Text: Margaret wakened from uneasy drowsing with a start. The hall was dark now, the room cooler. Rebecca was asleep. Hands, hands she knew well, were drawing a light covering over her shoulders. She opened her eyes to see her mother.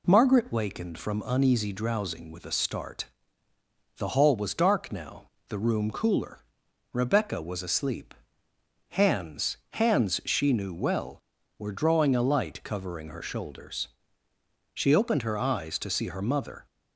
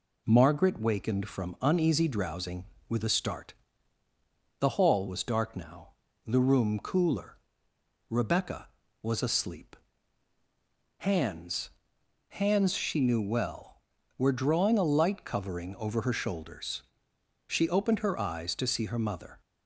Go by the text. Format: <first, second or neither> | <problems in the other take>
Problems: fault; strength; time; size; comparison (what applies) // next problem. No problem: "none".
second | skips "over"; at 13.0 s